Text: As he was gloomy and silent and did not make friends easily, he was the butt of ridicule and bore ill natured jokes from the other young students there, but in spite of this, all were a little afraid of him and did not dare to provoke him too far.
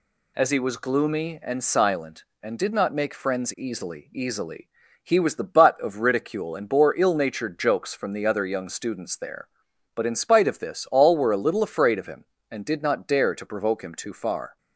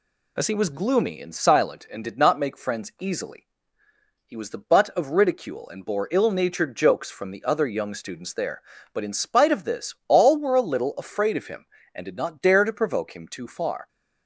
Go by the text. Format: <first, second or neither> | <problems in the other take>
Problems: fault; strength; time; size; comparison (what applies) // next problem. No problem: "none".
second | says "easily" twice; at 4.1 s